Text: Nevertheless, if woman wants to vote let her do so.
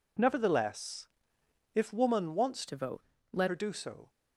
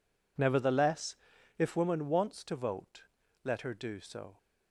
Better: second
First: changes voice from "to" to "let"; from 2.6 to 3.4 s; 0.8 s long // pauses between "vote" and "let"; slight; at 3.0 s; 0.30 s long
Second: pauses between "vote" and "let"; at 3.0 s; 0.40 s long

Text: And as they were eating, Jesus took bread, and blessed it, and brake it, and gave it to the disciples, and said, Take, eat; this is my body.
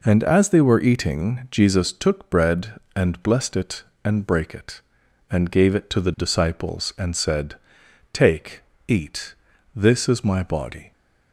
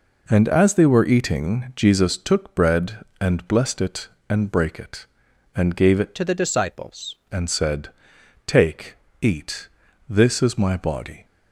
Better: first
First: none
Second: changes voice from "to" to "disciples"; from 6.1 to 7.1 s; 1.0 s long

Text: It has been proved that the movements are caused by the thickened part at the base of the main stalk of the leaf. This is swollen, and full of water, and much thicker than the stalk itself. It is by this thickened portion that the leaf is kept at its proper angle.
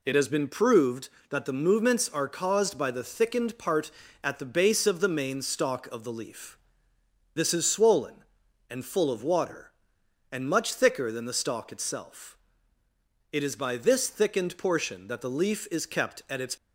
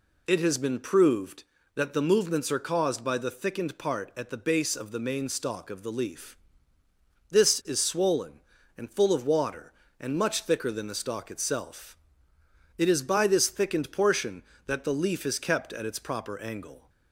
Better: second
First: stops before "proper angle"; at 16.5 s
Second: none

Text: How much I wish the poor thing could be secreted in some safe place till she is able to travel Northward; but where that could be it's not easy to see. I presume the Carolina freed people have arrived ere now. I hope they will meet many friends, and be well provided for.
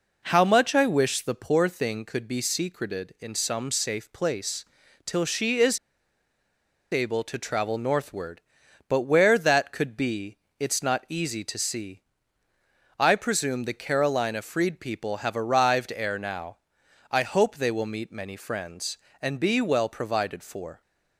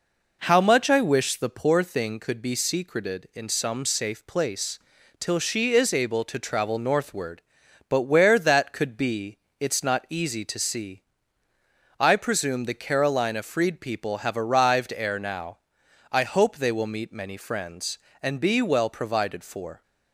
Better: second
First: pauses between "place" and "till"; at 4.6 s; 0.40 s long // pauses between "is" and "able"; at 5.7 s; 1.1 s long // pauses between "be" and "it's"; slight; at 10.3 s; 0.22 s long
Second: pauses between "place" and "till"; at 4.7 s; 0.40 s long // pauses between "be" and "it's"; slight; at 9.3 s; 0.22 s long

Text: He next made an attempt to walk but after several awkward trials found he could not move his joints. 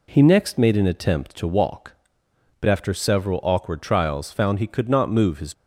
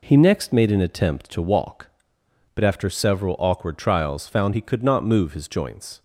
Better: second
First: stops before "joints"; at 5.5 s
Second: none

